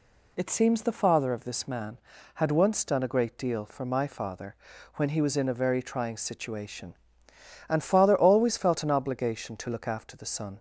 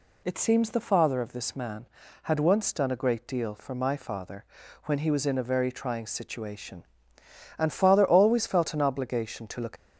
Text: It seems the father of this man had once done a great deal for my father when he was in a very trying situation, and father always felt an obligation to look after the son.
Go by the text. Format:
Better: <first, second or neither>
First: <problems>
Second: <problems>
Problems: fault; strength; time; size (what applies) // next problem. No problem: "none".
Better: first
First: pauses between "father" and "when"; at 4.5 s; 0.40 s long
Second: pauses between "father" and "when"; at 4.4 s; 0.40 s long // stops before "after the son"; at 9.7 s